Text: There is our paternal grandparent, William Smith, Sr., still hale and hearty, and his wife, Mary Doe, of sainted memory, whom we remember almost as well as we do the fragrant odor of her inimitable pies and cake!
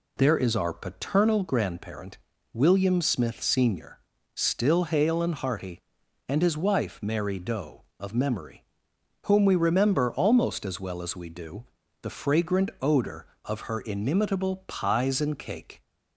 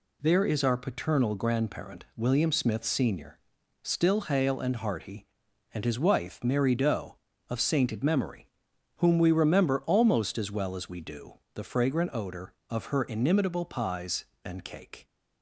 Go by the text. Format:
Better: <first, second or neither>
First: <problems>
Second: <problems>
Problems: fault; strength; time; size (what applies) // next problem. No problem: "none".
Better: second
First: skips "sainted"; at 8.1 s // pauses between "do" and "the"; at 11.6 s; 0.38 s long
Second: pauses between "do" and "the"; slight; at 11.3 s; 0.16 s long